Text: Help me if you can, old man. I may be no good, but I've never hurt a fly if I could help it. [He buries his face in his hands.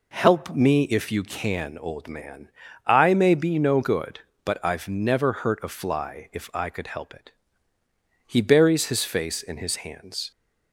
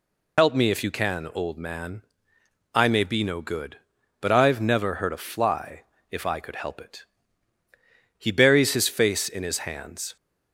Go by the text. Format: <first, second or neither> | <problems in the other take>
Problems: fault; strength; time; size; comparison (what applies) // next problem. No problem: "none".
first | loses the start of "Help"; at 0.3 s; 65 ms // pauses between "fly" and "if"; slight; at 5.8 s; 0.28 s long